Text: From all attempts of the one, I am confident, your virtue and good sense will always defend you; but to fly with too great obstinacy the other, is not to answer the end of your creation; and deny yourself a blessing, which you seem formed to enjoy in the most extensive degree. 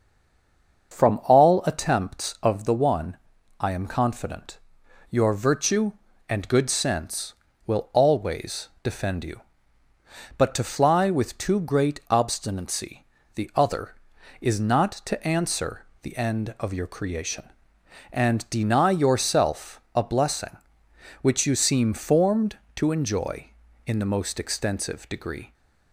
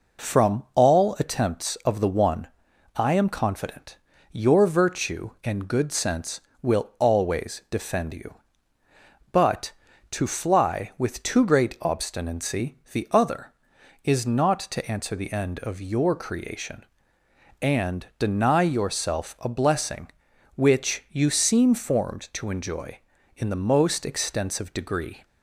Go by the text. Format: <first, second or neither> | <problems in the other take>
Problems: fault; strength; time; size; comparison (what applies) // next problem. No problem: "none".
second | stays silent before the first word; slight; until 0.9 s; 0.9 s long // starts louder than the rest; until 1.9 s; 6.5 dB // pauses between "always" and "defend"; slight; at 8.6 s; 0.16 s long // pauses between "obstinacy" and "the"; slight; at 13.0 s; 0.30 s long // pauses between "answer" and "the"; slight; at 15.8 s; 0.16 s long